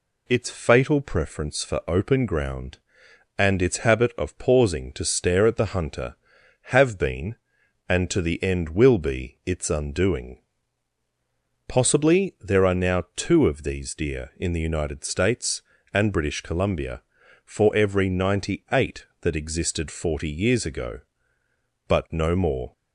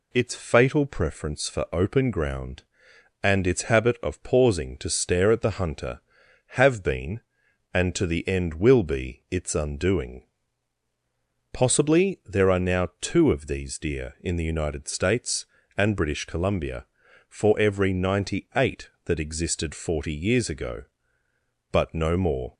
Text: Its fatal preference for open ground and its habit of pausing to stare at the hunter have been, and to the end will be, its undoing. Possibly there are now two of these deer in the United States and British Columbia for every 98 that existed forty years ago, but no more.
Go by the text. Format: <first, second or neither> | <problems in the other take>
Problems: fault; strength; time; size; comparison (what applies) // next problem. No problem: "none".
neither | none